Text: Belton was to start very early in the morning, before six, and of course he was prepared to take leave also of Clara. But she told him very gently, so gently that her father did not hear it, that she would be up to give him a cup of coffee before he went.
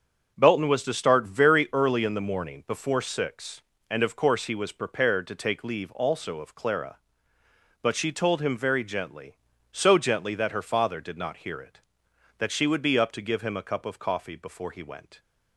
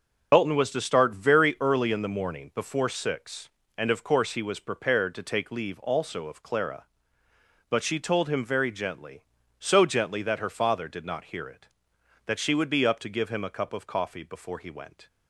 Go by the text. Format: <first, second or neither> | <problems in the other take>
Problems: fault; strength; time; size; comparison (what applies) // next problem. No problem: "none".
first | loses the start of "Belton"; at 0.3 s; 90 ms